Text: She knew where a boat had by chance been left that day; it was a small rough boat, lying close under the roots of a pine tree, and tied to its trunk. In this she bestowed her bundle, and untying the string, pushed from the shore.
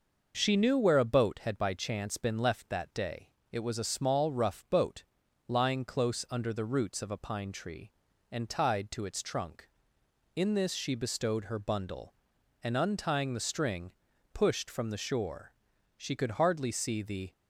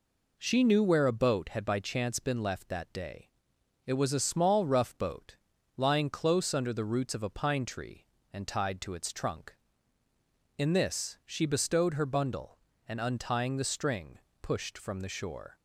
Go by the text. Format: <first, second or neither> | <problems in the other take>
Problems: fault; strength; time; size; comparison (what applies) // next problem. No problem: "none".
second | goes on to say "She could hardly see the"; from 15.9 s on; 1.3 s long